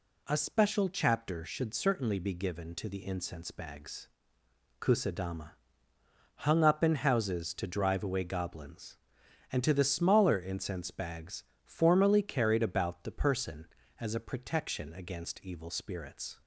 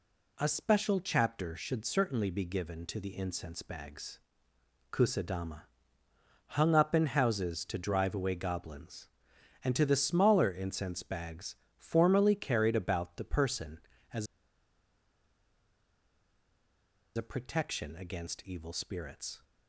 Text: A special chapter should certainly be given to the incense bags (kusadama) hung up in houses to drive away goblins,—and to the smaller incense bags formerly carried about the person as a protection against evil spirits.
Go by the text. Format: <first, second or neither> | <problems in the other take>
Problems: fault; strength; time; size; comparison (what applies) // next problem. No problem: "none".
first | pauses between "bags" and "formerly"; slight; at 11.5 s; 0.24 s long; slight in the first // pauses between "as" and "a"; strong; at 14.2 s; 2.8 s long